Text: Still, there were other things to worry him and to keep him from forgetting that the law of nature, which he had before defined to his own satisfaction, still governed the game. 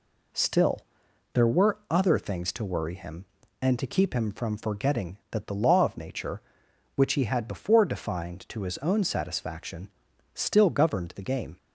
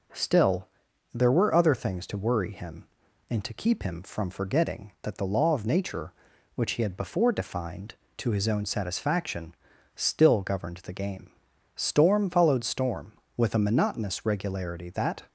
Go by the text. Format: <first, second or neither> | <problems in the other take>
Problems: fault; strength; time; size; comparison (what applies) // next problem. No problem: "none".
first | goes on to say "Storm followed storm with a monotonous regularity that"; strong; from 11.7 s on; 3.5 s long